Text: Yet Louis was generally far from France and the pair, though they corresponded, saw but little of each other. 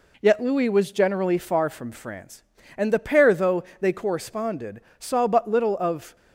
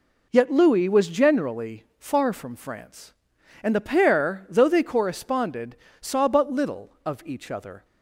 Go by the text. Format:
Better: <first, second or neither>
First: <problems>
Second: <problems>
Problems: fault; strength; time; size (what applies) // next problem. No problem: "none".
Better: second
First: pauses between "though" and "they"; slight; at 3.6 s; 0.16 s long // stops before "each other"; at 6.1 s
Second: none